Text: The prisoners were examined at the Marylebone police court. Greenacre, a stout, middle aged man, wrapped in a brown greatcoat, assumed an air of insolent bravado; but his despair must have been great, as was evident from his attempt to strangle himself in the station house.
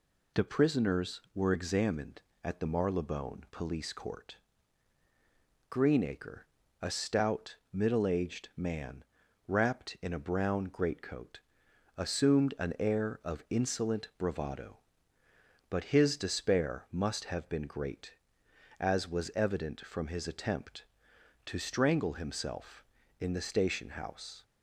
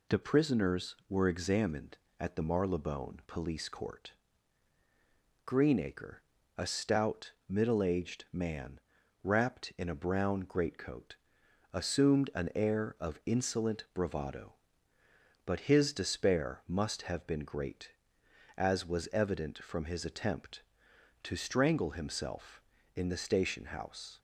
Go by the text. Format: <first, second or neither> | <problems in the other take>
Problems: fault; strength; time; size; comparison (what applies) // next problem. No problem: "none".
neither | none